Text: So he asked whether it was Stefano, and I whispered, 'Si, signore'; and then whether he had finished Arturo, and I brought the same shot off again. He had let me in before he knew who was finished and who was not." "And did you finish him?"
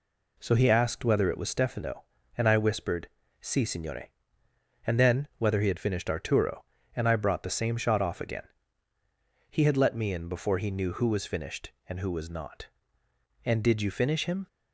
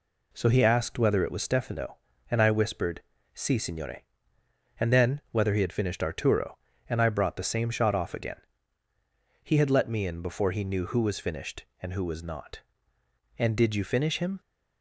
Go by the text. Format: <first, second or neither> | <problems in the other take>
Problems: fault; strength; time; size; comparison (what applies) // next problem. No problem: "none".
neither | none